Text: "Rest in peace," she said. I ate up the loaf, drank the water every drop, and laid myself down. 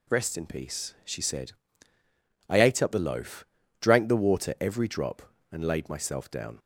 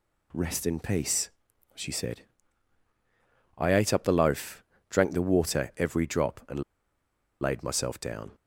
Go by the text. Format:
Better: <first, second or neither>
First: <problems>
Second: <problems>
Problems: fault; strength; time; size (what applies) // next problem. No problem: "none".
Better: first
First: none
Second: pauses between "and" and "laid"; noticeable; at 6.6 s; 0.77 s long